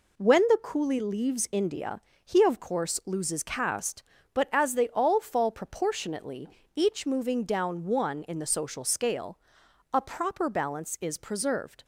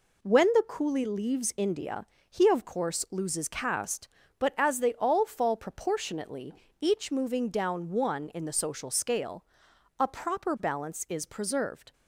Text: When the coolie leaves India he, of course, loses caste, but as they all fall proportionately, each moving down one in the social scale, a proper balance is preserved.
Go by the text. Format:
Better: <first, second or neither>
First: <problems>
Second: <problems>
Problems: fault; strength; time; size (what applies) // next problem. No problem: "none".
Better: neither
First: pauses between "India" and "he"; slight; at 1.9 s; 0.28 s long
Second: pauses between "India" and "he"; slight; at 2.0 s; 0.28 s long